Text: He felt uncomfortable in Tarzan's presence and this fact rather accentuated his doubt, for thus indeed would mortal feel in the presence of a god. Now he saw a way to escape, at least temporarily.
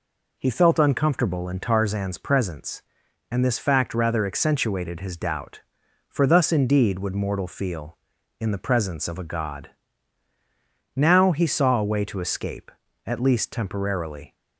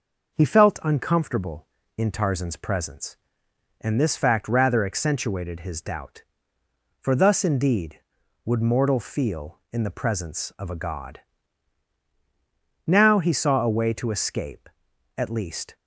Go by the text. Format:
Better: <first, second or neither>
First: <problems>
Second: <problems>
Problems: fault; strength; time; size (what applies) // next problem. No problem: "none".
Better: first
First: none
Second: starts louder than the rest; noticeable; until 1.3 s; 6 dB // stops before "temporarily"; at 15.7 s